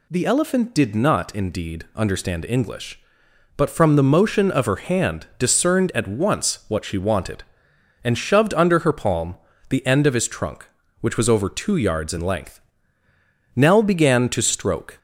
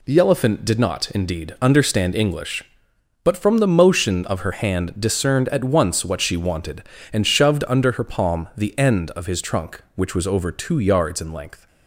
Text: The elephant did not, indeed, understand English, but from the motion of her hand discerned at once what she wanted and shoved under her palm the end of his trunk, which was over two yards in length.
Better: second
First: pauses between "palm" and "the"; slight; at 9.3 s; 0.34 s long // goes on to say "Nell began to stroke"; from 13.5 s on; 1.4 s long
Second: none

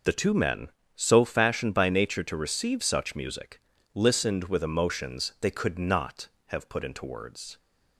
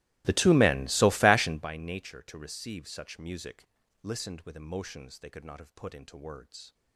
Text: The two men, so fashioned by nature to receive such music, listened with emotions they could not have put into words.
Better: first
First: none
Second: starts louder than the rest; strong; until 1.7 s; 18.5 dB

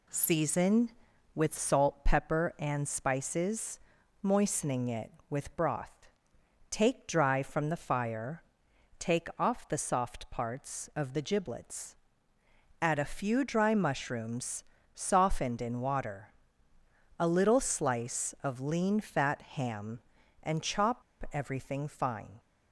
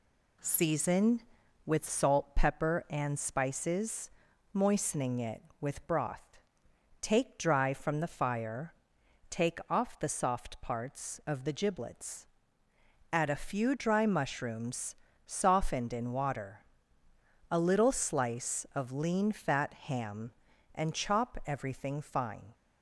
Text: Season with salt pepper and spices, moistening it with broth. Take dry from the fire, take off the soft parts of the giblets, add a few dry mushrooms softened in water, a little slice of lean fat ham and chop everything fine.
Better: second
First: pauses between "mushrooms" and "softened"; slight; at 14.6 s; 0.30 s long // pauses between "chop" and "everything"; slight; at 21.0 s; 0.30 s long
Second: pauses between "mushrooms" and "softened"; slight; at 14.9 s; 0.30 s long

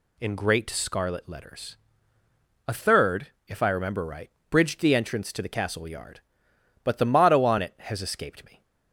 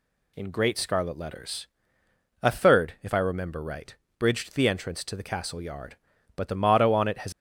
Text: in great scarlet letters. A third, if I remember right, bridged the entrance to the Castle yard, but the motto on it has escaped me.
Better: first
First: none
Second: stops before "escaped me"; at 7.3 s

